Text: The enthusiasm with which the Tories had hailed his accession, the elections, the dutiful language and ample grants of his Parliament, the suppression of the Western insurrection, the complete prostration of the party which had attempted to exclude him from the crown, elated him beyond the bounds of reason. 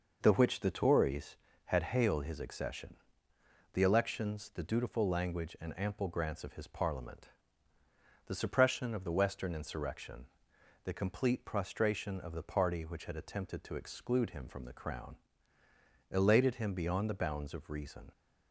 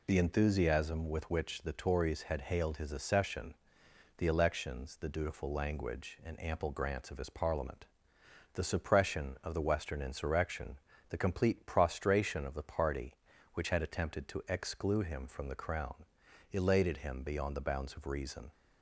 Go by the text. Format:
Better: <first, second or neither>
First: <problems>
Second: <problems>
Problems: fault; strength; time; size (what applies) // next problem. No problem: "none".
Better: second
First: skips "enthusiasm with"; at 0.3 s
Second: none